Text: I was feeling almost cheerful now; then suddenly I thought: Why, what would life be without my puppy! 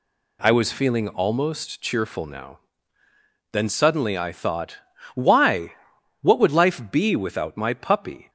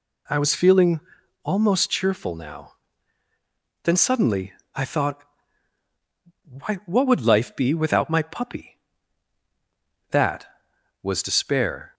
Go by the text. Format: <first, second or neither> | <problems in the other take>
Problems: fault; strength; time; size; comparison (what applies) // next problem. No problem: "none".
first | pauses between "feeling" and "almost"; at 1.0 s; 0.45 s long // pauses between "suddenly" and "I"; slight; at 4.5 s; 0.24 s long // goes on to say "That was despair"; strong; from 10.0 s on; 1.8 s long